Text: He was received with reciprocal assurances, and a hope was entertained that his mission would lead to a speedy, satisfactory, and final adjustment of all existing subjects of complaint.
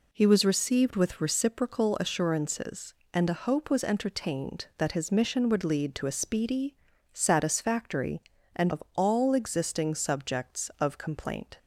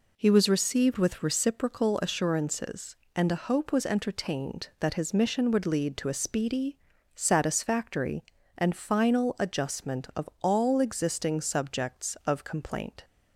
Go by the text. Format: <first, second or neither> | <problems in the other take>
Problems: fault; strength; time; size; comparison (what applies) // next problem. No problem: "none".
second | skips "final adjustment"; at 8.7 s